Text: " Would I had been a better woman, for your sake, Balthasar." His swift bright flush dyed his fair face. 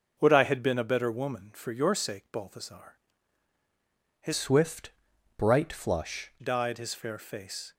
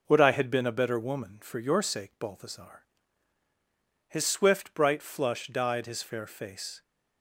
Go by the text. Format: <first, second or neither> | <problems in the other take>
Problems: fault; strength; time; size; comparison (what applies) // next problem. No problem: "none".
second | changes voice from "swift" to "flush"; from 4.3 to 6.3 s; 2.0 s long // pauses between "swift" and "bright"; noticeable; at 4.9 s; 0.46 s long